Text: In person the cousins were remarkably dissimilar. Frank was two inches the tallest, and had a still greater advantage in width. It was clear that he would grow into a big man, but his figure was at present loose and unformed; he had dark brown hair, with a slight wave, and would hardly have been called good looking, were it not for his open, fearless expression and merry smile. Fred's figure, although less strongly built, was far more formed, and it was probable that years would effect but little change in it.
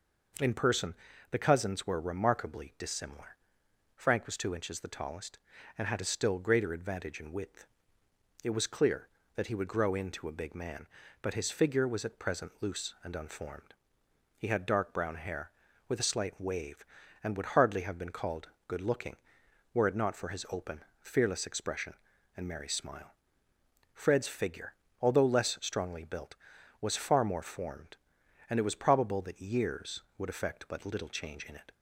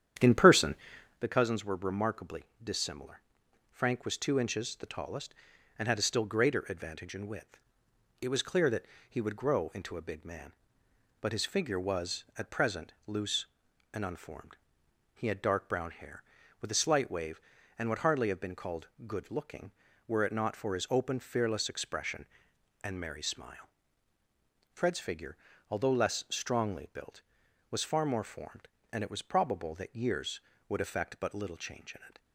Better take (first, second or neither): first